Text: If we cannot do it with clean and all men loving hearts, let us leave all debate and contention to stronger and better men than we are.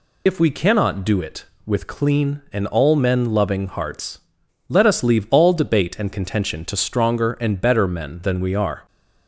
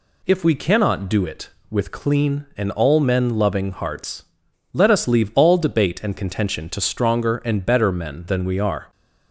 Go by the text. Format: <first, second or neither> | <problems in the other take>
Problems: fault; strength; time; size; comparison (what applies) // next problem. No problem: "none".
second | loses the start of "If"; at 0.2 s; 60 ms